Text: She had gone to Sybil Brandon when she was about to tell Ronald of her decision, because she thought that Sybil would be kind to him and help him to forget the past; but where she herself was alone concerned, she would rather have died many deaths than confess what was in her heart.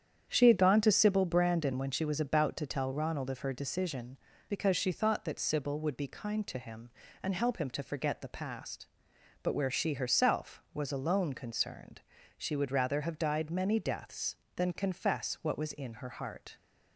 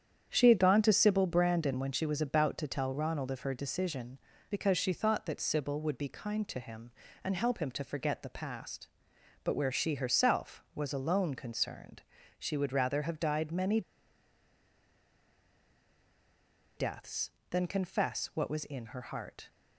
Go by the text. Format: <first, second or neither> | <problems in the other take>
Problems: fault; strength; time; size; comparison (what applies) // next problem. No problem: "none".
first | starts louder than the rest; strong; until 1.3 s; 8.5 dB; strong in the first // pauses between "many" and "deaths"; strong; at 13.8 s; 2.9 s long